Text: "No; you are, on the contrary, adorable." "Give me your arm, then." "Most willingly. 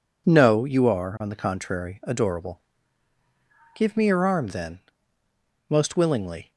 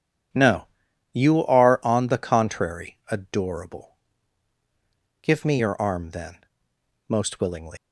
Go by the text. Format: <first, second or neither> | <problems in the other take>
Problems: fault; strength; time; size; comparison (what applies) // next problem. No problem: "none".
first | leaves "willingly" unfinished; at 7.7 s; 120 ms